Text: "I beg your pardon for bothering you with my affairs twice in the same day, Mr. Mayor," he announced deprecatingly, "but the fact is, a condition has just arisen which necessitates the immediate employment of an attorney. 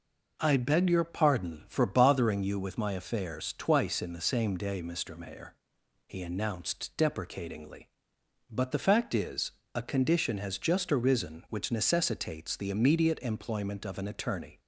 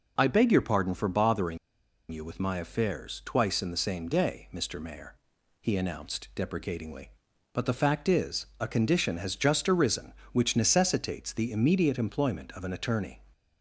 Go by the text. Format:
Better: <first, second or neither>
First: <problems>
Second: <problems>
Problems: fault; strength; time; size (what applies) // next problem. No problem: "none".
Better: first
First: none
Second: pauses between "bothering" and "you"; noticeable; at 1.5 s; 0.53 s long